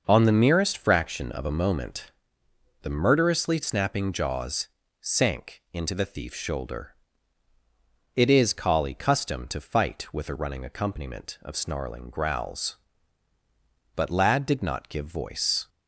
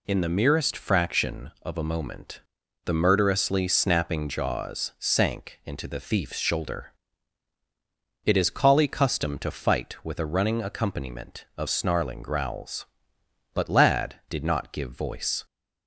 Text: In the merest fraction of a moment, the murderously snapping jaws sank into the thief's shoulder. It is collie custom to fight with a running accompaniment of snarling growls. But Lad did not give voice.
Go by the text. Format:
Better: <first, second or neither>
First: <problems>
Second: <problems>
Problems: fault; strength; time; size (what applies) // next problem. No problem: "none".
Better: second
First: says "On" for "In"; at 0.0 s // pauses between "jaws" and "sank"; slight; at 4.6 s; 0.32 s long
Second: none